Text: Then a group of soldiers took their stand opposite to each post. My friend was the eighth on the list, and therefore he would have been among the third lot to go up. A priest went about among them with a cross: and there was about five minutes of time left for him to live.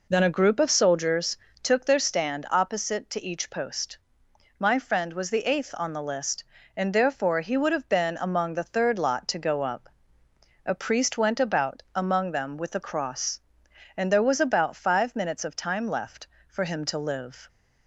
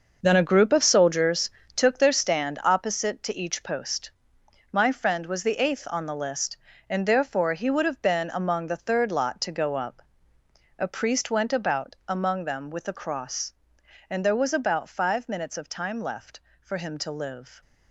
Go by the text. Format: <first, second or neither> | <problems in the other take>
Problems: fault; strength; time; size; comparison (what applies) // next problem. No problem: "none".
first | gets quieter; strong; throughout; 10 dB // pauses between "soldiers" and "took"; slight; at 1.5 s; 0.24 s long; slight in the first